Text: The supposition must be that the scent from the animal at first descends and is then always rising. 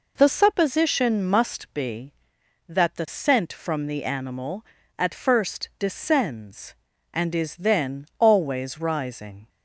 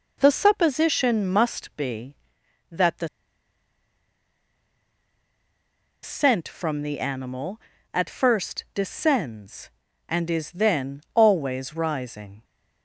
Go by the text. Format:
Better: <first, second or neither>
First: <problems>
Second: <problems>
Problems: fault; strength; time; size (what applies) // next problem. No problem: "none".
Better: first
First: none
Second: pauses between "the" and "scent"; strong; at 3.0 s; 2.9 s long